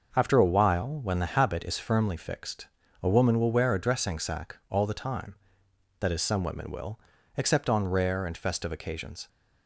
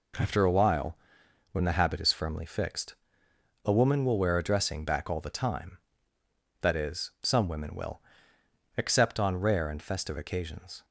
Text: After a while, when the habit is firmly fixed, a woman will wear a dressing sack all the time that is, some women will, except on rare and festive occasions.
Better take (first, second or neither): first